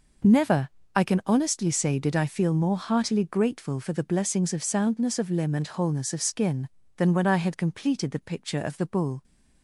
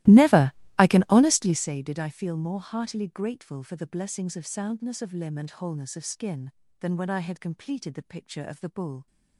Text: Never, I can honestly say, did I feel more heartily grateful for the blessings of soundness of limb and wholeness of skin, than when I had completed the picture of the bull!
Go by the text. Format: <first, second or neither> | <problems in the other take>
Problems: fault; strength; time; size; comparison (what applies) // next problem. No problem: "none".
first | starts louder than the rest; strong; until 1.7 s; 17 dB